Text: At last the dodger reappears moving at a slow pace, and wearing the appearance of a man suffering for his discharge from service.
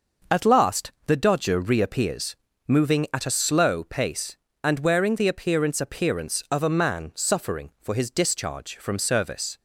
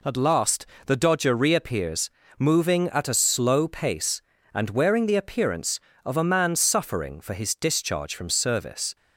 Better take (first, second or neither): second